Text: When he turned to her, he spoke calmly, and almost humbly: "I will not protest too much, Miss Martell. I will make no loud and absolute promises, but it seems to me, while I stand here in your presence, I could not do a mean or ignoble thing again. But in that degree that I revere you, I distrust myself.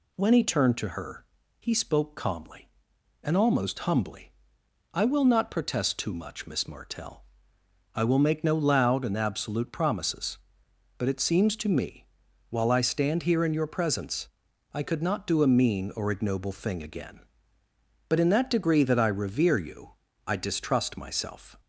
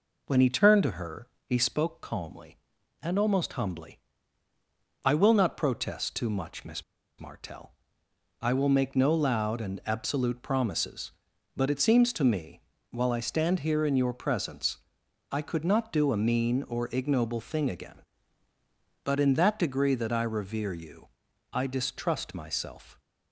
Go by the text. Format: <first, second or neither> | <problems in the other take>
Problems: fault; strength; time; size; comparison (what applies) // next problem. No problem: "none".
first | pauses between "Miss" and "Martell"; slight; at 6.8 s; 0.35 s long